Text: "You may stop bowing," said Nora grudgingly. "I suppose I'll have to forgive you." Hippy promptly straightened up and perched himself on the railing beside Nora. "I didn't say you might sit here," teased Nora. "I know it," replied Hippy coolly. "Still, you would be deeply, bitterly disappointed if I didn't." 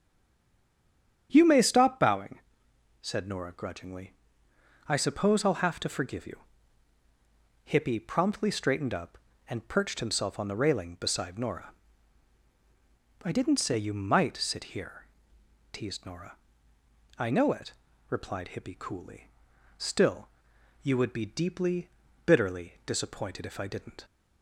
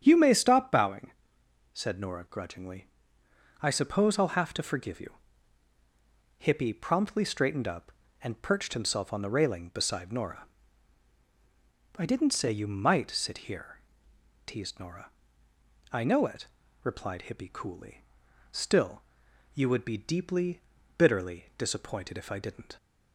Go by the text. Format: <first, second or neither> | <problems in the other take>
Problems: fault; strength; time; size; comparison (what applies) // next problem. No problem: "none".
second | stays silent before the first word; noticeable; until 1.2 s; 1.2 s long // starts louder than the rest; strong; until 2.3 s; 8.5 dB; strong in the second